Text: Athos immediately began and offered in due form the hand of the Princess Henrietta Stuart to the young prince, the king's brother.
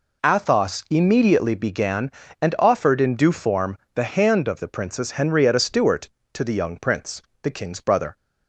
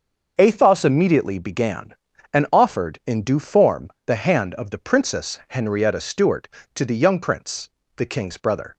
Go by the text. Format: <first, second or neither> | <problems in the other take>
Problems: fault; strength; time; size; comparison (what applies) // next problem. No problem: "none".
neither | pauses between "form" and "the"; slight; the same in both